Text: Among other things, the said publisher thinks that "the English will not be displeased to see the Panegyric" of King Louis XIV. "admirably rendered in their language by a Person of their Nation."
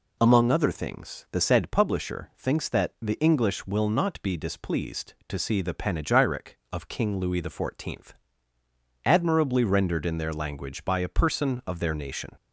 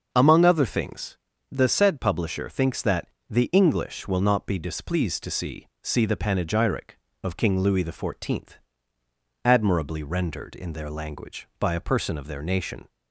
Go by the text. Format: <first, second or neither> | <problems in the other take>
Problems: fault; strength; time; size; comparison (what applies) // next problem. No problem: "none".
first | starts louder than the rest; until 1.1 s; 6.5 dB // pauses between "that" and "the"; slight; at 3.0 s; 0.22 s long // says "see" twice; at 5.8 s